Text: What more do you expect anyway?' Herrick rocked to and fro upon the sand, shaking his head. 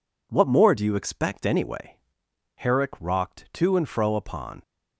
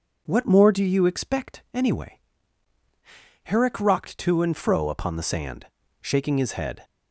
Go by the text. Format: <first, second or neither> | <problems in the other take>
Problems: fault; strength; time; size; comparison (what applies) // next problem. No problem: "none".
second | stops before "the sand shaking his head"; at 4.6 s